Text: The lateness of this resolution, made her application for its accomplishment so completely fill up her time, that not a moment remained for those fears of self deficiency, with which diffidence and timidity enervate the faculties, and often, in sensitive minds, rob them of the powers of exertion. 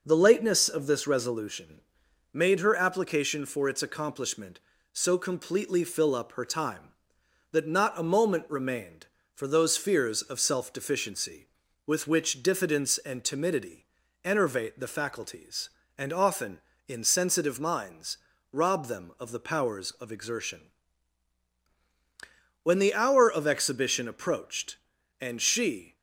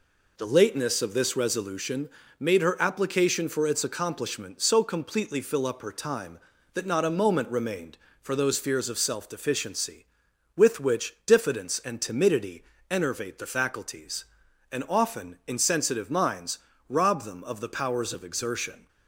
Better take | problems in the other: second | pauses between "timidity" and "enervate"; slight; at 13.8 s; 0.36 s long; slight in the second // goes on to say "When the hour of exhibition approached and she"; strong; from 22.6 s on; 3.3 s long

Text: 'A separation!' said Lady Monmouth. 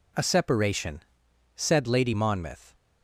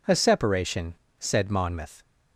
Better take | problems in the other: first | skips "Lady"; at 1.4 s

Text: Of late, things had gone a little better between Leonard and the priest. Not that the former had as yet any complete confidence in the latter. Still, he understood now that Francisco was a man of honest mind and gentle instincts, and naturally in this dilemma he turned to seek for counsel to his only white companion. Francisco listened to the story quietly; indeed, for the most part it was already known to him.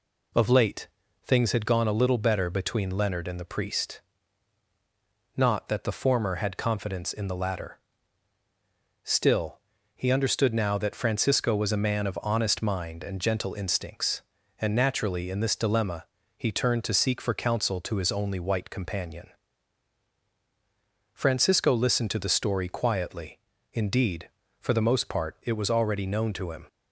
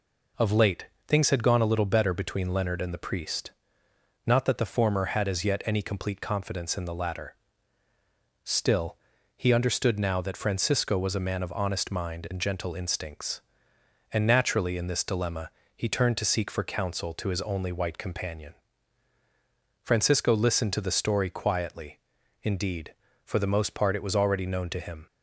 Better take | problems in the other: second | skips "as yet any complete"; at 6.5 s // pauses between "dilemma" and "he"; slight; at 16.0 s; 0.30 s long; slight in the second

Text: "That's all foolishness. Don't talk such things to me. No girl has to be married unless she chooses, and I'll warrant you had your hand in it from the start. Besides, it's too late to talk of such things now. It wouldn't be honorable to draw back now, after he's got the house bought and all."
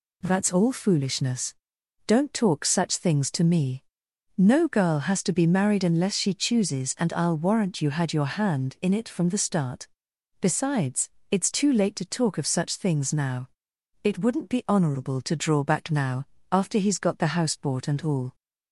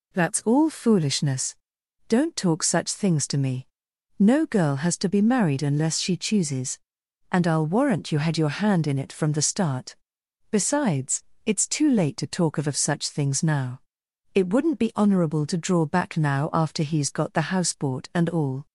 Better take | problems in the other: first | says "of" twice; at 12.6 s

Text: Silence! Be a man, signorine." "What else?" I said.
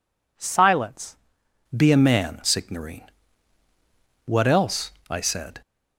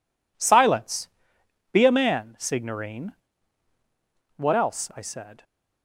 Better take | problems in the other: second | changes voice at "Be"; from 1.7 s on; 3.9 s long

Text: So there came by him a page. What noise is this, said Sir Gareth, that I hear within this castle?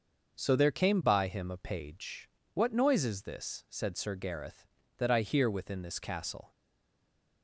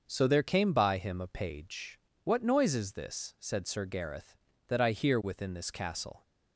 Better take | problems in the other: second | starts louder than the rest; until 1.4 s; 6 dB; also in the second // stays silent after the last word; slight; from 6.5 s on; 0.9 s long

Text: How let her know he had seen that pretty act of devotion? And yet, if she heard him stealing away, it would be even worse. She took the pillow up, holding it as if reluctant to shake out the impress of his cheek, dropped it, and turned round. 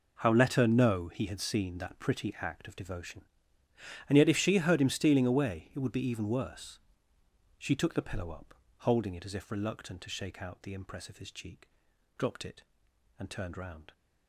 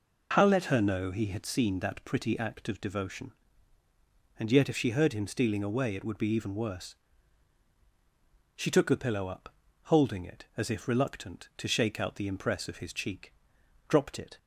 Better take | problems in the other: first | stops before "and turned round"; at 14.3 s

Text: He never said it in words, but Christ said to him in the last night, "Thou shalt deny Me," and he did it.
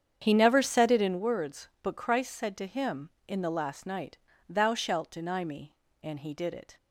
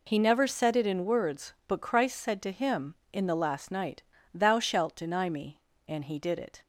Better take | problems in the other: second | starts louder than the rest; strong; until 1.2 s; 8 dB

